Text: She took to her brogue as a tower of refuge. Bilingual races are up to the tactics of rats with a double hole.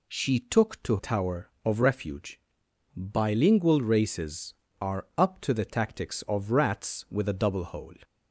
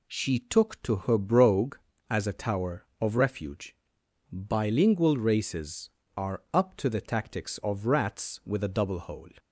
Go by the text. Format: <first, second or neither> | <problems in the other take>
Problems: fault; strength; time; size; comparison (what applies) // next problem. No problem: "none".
second | skips "her brogue as a"; at 0.9 s